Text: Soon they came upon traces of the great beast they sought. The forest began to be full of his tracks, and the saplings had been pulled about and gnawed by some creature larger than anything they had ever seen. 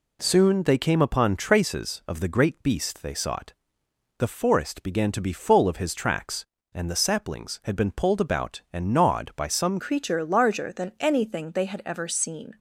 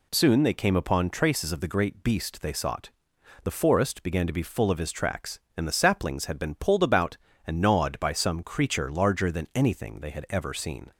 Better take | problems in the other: second | changes voice at "creature"; from 9.8 s on; 2.7 s long

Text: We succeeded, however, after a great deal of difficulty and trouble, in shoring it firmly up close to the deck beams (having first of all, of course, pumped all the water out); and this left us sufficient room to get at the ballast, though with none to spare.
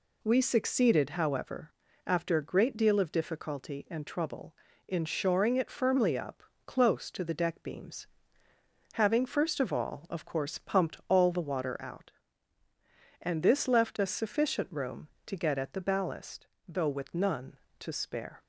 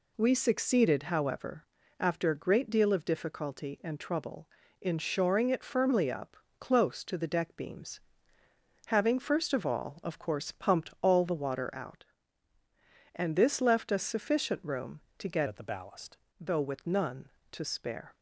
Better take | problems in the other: first | pauses between "up" and "close"; slight; at 6.3 s; 0.22 s long; slight in the first // changes voice from "at" to "ballast"; from 15.4 to 16.1 s; 0.7 s long

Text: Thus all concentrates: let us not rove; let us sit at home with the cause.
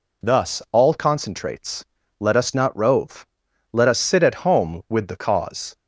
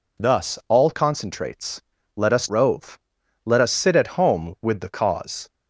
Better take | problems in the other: first | skips "not"; at 2.5 s

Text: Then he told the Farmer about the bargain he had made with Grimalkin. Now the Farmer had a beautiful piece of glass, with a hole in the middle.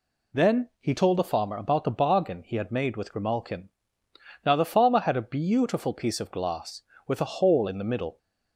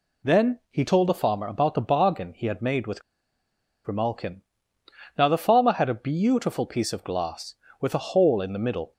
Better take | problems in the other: first | pauses between "with" and "Grimalkin"; noticeable; at 3.0 s; 0.82 s long

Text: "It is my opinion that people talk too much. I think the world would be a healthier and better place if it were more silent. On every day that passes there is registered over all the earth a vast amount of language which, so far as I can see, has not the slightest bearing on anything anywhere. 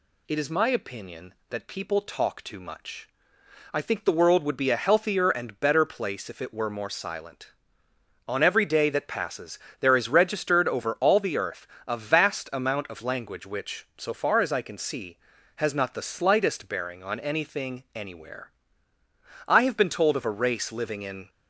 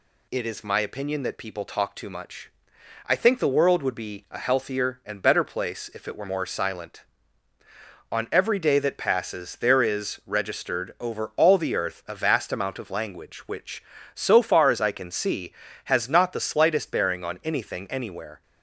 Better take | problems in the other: second | pauses between "passes" and "there"; slight; at 9.5 s; 0.22 s long // pauses between "earth" and "a"; slight; at 11.6 s; 0.20 s long // goes on to say "I have been told of a race living in"; strong; from 19.4 s on; 1.8 s long

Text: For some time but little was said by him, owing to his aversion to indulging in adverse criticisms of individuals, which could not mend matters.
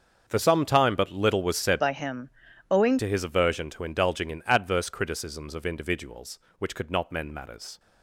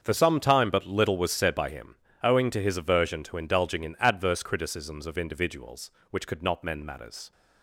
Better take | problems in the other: second | starts louder than the rest; until 1.2 s; 7 dB; also in the second // changes voice from "by" to "owing"; from 1.8 to 2.9 s; 1.1 s long

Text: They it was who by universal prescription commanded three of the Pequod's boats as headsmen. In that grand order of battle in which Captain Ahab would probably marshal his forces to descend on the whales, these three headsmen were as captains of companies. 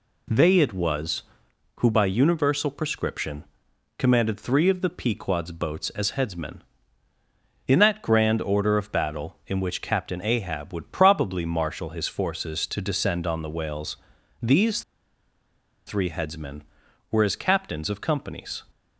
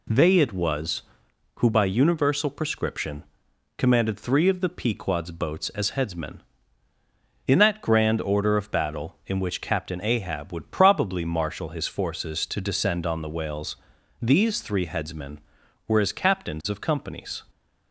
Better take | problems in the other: second | pauses between "prescription" and "commanded"; noticeable; at 3.4 s; 0.52 s long; noticeable in the second // pauses between "these" and "three"; at 14.8 s; 1.0 s long

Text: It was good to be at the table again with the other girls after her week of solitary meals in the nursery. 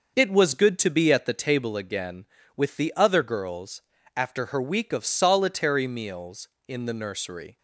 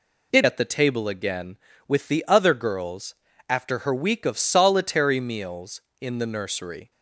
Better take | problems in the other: first | skips "was good to be"; at 0.4 s // pauses between "girls" and "after"; slight; at 3.1 s; 0.34 s long; slight in the first

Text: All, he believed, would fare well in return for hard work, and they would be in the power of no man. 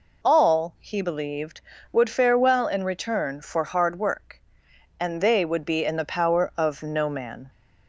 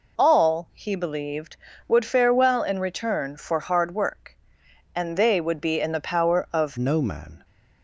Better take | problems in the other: first | changes voice at "no"; from 6.7 s on; 0.7 s long

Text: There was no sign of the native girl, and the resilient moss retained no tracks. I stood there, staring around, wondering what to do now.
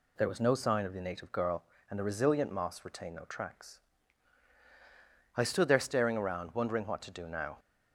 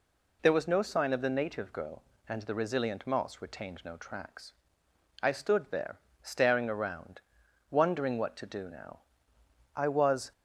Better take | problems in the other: first | goes on to say "I was"; from 9.7 s on; 0.56 s long

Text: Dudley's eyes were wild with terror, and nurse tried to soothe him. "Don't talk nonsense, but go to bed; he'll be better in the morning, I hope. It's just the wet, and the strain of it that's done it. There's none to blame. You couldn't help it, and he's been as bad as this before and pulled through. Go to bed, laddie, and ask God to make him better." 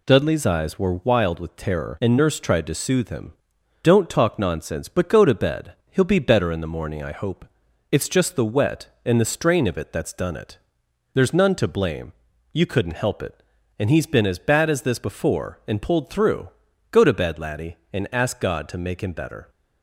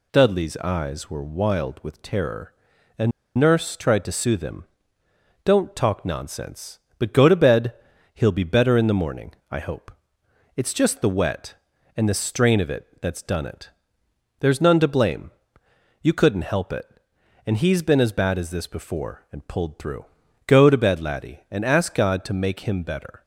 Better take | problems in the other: first | pauses between "and" and "nurse"; slight; at 3.1 s; 0.27 s long

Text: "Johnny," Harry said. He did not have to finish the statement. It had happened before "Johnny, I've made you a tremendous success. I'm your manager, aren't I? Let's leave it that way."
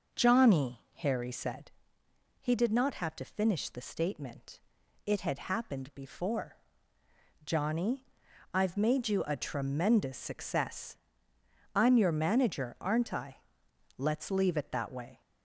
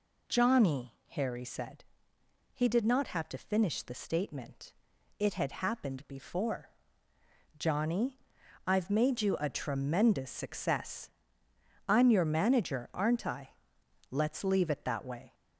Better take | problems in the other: second | starts louder than the rest; noticeable; until 1.9 s; 5.5 dB // pauses between "before" and "Johnny"; noticeable; at 6.5 s; 0.88 s long; noticeable in the second

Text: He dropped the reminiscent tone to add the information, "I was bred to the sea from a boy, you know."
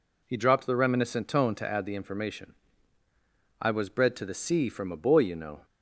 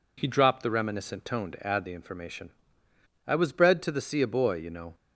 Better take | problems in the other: first | skips "from"; at 4.2 s

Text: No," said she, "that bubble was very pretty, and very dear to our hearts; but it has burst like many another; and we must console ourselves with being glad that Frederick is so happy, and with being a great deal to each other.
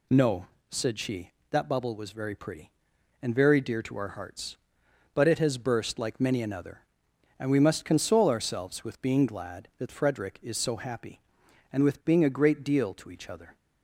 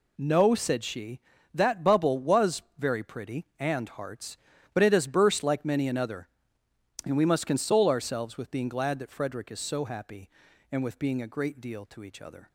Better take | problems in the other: first | pauses between "was" and "very"; slight; at 2.6 s; 0.16 s long // skips "very dear to our"; at 3.8 s

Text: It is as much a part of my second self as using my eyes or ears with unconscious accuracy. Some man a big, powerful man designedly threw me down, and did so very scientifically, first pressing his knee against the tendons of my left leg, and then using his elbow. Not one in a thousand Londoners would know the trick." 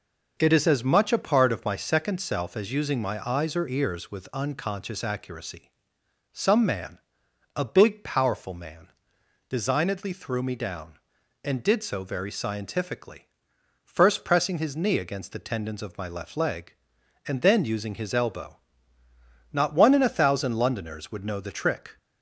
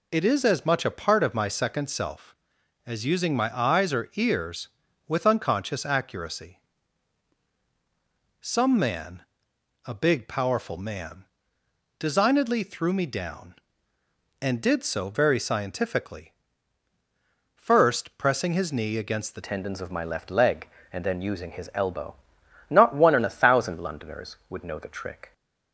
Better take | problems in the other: first | pauses between "man" and "a"; noticeable; at 9.2 s; 0.62 s long; noticeable in the first // pauses between "man" and "designedly"; noticeable; at 11.2 s; 0.72 s long; noticeable in the first // changes voice at "tendons"; from 19.4 s on; 5.9 s long

